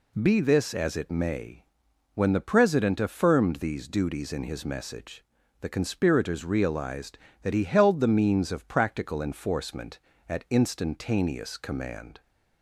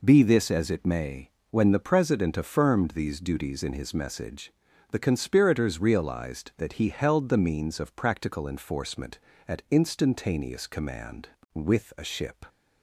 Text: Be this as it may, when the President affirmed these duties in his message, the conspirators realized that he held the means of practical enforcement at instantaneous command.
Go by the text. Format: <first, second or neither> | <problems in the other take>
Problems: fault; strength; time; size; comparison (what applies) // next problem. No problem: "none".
first | goes on to say "With a ship"; noticeable; from 11.5 s on; 0.92 s long